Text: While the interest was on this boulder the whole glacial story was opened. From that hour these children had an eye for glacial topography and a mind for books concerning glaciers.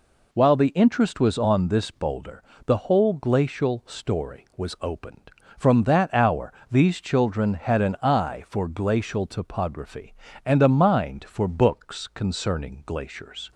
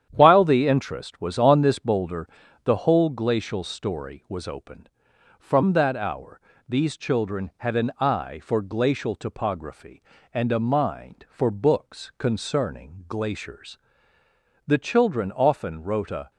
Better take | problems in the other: first | starts louder than the rest; strong; until 1.1 s; 9.5 dB // pauses between "boulder" and "the"; slight; at 2.2 s; 0.36 s long; slight in the first // pauses between "hour" and "these"; slight; at 6.4 s; 0.28 s long; slight in the first // goes on to say "The children often wrote a"; from 14.6 s on; 1.6 s long

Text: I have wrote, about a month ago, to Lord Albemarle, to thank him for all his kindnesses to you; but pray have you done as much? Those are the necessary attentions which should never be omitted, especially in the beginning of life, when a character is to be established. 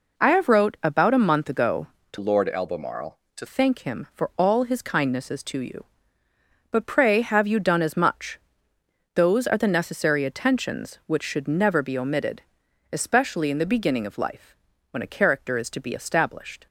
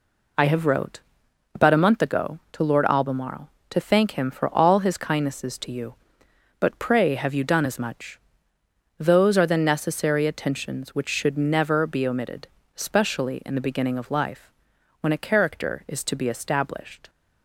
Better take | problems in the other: second | changes voice from "Lord" to "to"; from 2.1 to 3.4 s; 1.3 s long

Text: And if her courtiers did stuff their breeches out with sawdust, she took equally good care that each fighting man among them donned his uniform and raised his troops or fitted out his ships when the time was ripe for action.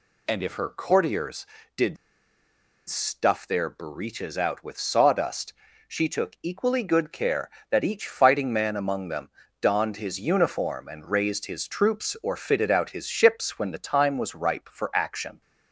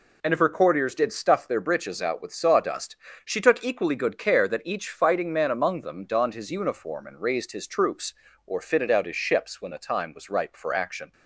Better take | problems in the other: second | pauses between "did" and "stuff"; noticeable; at 1.9 s; 0.91 s long // pauses between "them" and "donned"; slight; at 9.3 s; 0.30 s long

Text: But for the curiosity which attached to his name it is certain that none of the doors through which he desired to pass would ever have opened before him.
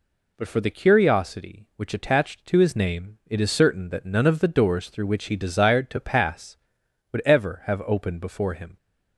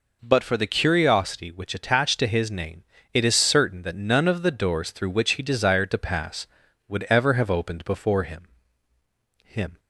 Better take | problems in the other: first | pauses between "name" and "it"; slight; at 2.8 s; 0.28 s long // says "him" twice; at 9.4 s

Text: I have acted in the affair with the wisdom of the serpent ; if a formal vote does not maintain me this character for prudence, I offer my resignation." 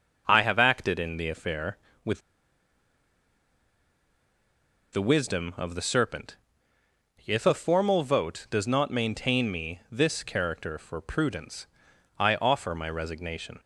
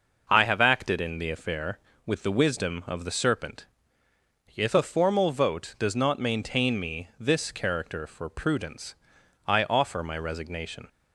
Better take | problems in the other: second | pauses between "with" and "the"; strong; at 2.2 s; 2.7 s long

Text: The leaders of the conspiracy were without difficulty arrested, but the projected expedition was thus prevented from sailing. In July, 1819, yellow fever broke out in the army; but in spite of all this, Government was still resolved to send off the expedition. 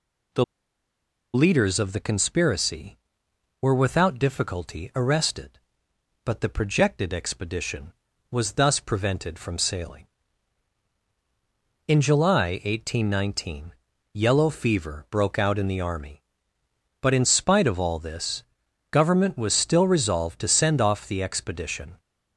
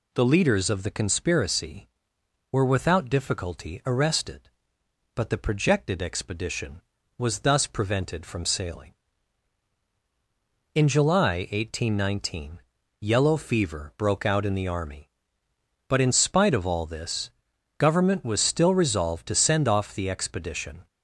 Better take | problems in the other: second | pauses between "The" and "leaders"; noticeable; at 0.4 s; 0.90 s long

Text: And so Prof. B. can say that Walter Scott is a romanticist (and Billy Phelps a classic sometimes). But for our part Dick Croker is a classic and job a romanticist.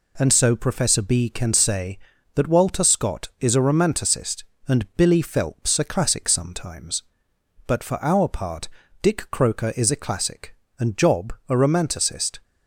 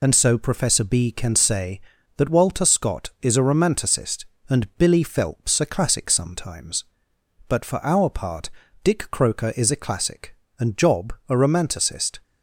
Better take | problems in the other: first | loses the start of "And"; at 0.0 s; 50 ms // pauses between "part" and "Dick"; slight; at 8.4 s; 0.34 s long; slight in the first

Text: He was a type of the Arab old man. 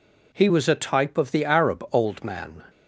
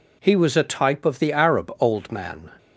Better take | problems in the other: neither | none

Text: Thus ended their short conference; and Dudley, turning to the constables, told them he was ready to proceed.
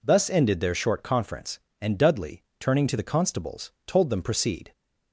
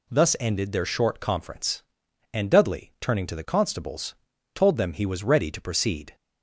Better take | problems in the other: second | skips "he was ready to"; at 4.2 s

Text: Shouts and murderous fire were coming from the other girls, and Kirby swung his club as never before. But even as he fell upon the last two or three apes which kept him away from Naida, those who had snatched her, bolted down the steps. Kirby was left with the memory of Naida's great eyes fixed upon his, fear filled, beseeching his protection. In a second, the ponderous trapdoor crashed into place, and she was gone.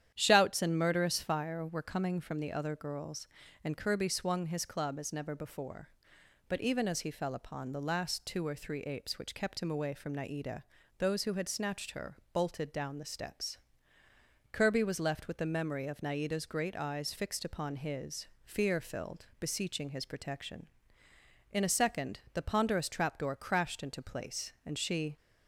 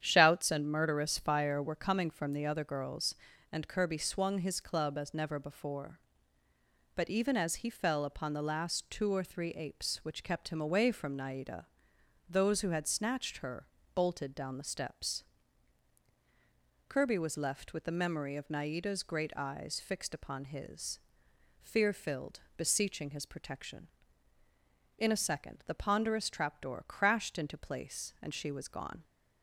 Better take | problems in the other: second | starts louder than the rest; strong; until 1.1 s; 10 dB; strong in the second // stops before "was gone"; at 25.1 s

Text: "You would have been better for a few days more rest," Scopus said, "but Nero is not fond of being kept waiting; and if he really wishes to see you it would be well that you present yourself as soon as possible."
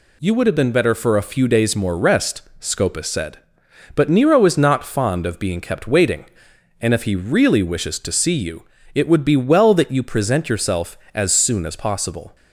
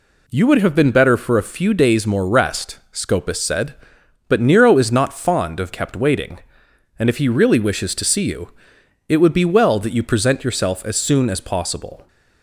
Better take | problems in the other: first | skips "being"; at 5.7 s // pauses between "you" and "it"; noticeable; at 8.4 s; 0.58 s long; slight in the first

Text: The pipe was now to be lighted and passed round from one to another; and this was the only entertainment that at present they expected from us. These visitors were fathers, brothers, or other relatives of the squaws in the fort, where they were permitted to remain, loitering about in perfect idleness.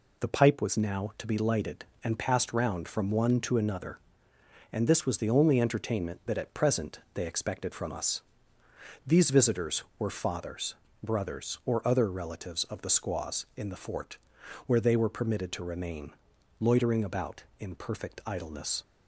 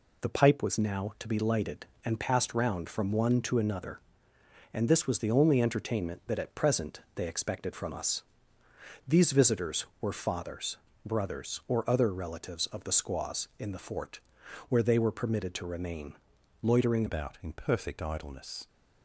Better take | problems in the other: first | pauses between "present" and "they"; slight; at 6.9 s; 0.16 s long; slight in the first // changes voice at "about"; from 17.0 s on; 1.6 s long

